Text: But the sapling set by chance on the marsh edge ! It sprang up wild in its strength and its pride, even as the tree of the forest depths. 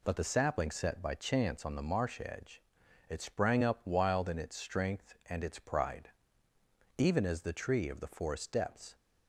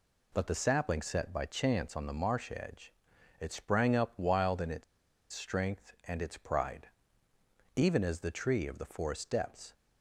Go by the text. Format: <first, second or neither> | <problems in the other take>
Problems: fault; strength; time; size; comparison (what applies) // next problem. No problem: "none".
first | pauses between "its" and "strength"; noticeable; at 4.8 s; 0.48 s long